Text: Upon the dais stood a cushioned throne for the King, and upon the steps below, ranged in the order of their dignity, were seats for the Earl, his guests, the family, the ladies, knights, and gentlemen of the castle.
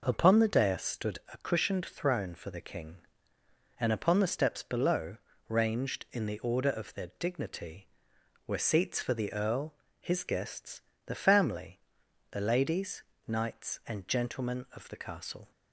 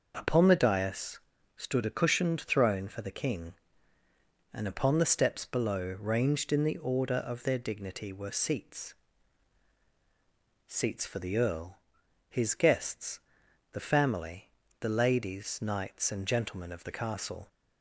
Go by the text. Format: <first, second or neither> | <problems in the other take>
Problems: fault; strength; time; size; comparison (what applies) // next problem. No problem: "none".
first | starts louder than the rest; noticeable; until 1.1 s; 6 dB // pauses between "dais" and "stood"; at 1.1 s; 0.38 s long // says "seats" twice; at 10.6 s